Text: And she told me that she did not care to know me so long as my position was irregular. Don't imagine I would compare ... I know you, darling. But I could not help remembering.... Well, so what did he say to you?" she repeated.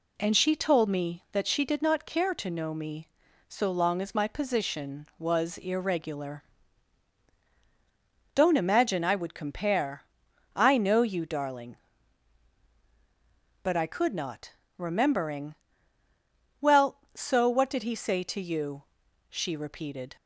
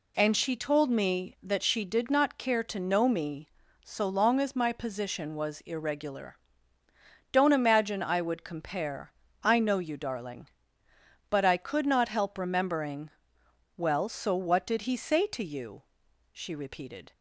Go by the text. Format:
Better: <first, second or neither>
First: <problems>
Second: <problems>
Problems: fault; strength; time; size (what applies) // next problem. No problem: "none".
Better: second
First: skips "help"; at 14.6 s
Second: none